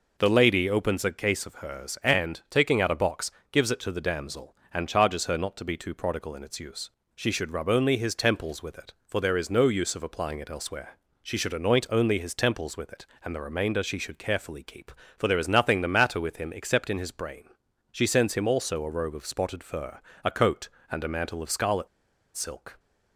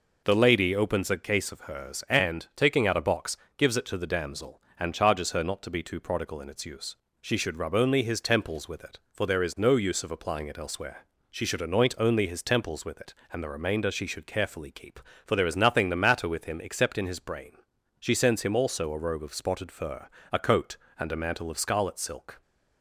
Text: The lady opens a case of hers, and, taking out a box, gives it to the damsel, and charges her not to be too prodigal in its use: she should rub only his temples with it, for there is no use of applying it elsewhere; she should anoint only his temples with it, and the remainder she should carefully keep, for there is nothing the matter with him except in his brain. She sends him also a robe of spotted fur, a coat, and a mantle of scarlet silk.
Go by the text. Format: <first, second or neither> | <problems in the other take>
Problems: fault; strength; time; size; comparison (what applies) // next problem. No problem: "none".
second | pauses between "scarlet" and "silk"; noticeable; at 21.8 s; 0.48 s long